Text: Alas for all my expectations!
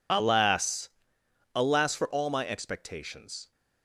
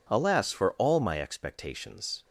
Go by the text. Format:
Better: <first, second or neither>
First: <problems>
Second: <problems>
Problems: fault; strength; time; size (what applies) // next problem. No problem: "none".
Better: second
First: says "Alas" twice; at 1.5 s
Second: none